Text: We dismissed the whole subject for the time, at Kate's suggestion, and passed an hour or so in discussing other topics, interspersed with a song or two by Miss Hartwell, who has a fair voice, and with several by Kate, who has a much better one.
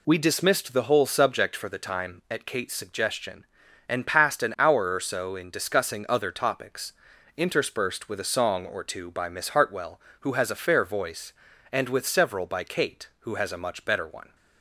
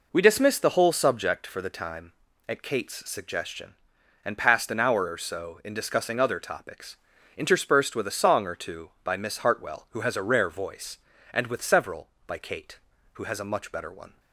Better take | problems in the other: first | says "rare" for "fair"; at 10.2 s

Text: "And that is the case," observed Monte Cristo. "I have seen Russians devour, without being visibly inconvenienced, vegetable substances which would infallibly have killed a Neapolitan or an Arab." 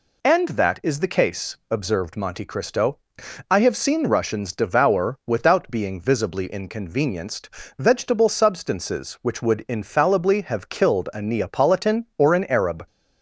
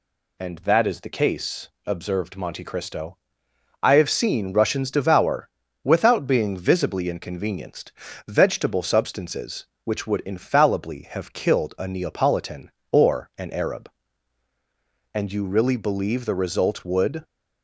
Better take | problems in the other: first | goes on to say "And you really believe the result would"; strong; from 15.1 s on; 2.1 s long

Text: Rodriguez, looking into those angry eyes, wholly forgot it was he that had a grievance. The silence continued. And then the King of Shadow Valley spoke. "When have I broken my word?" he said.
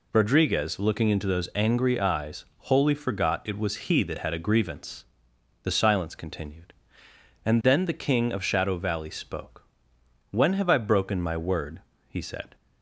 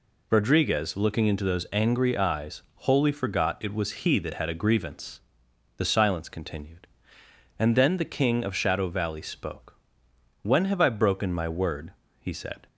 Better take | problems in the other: neither | none

